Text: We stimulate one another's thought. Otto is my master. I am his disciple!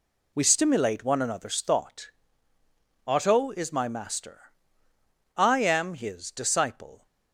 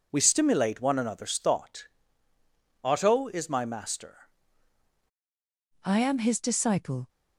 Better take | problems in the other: first | changes voice at "I"; from 5.8 s on; 1.2 s long

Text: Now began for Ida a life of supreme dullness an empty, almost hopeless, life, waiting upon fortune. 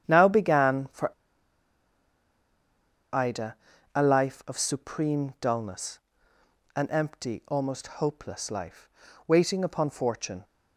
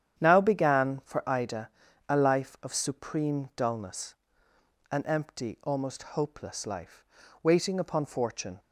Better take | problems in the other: second | starts louder than the rest; strong; until 1.1 s; 9.5 dB; strong in the second // pauses between "for" and "Ida"; strong; at 1.1 s; 2.0 s long // pauses between "Ida" and "a"; at 3.5 s; 0.40 s long; also in the second // pauses between "dullness" and "an"; noticeable; at 5.9 s; 0.76 s long; noticeable in the second

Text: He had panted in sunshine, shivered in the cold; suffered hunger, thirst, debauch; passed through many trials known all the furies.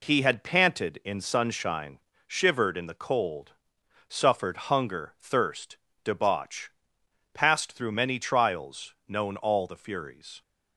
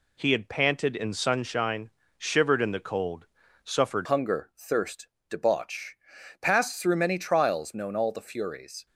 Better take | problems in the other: first | changes voice at "hunger"; from 4.0 s on; 4.8 s long

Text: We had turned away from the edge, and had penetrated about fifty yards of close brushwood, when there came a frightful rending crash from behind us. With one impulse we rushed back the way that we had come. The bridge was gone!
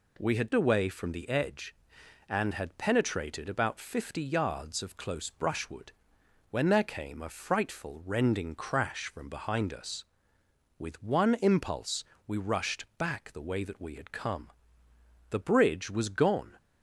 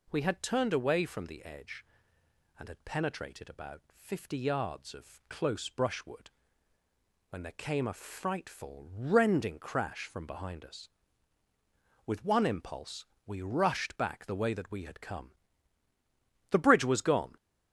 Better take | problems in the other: second | skips "turned"; at 0.5 s // pauses between "impulse" and "we"; slight; at 12.0 s; 0.24 s long; slight in the second

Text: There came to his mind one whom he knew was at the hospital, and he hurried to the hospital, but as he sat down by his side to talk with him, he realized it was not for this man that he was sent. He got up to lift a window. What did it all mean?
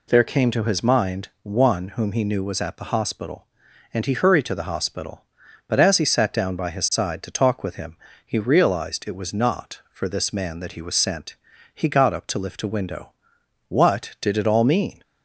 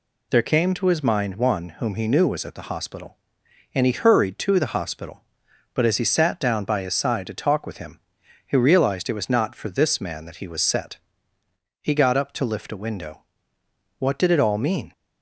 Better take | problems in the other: first | says "set" for "sent"; at 10.6 s

